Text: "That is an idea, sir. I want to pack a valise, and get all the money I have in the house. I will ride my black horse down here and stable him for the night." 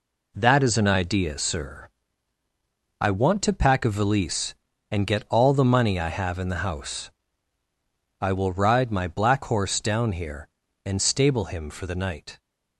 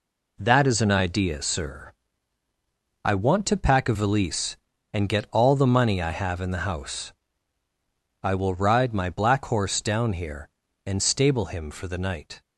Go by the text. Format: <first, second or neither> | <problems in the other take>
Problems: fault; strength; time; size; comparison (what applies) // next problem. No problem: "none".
neither | none